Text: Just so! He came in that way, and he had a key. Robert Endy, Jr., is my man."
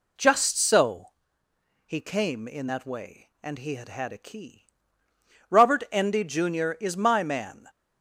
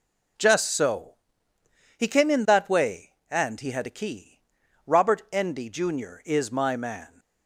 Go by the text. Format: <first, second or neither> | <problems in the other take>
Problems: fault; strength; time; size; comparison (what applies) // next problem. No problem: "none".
second | says "had" twice; at 3.8 s